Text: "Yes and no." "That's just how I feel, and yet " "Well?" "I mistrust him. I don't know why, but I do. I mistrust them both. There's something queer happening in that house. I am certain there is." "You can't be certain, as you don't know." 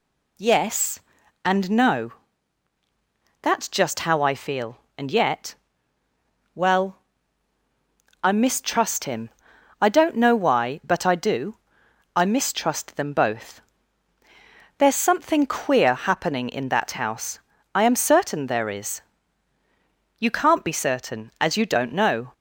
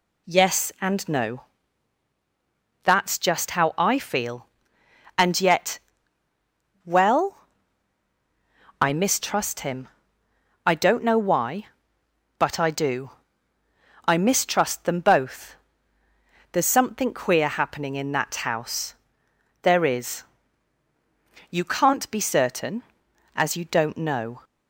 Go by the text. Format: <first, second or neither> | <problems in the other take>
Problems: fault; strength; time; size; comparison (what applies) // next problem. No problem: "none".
first | skips "I am certain"; at 19.2 s